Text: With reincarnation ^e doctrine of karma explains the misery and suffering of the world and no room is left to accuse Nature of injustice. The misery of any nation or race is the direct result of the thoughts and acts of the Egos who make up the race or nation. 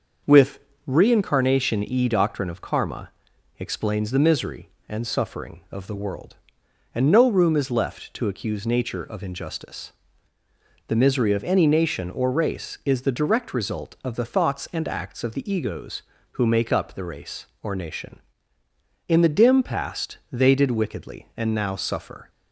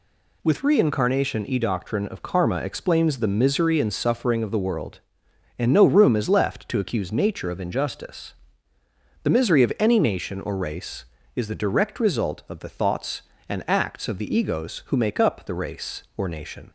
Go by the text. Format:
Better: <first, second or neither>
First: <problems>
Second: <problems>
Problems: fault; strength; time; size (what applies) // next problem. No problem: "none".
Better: second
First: starts louder than the rest; until 1.5 s; 6 dB // pauses between "With" and "reincarnation"; slight; at 0.5 s; 0.26 s long // pauses between "karma" and "explains"; noticeable; at 3.0 s; 0.50 s long // goes on to say "In the dim past they did wickedly and now suffer"; strong; from 19.0 s on; 3.2 s long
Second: none